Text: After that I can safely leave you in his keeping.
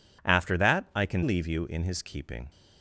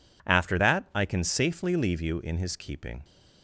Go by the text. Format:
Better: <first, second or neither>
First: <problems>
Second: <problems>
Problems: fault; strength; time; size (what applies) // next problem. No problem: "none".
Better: second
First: skips "safely"; at 1.2 s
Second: none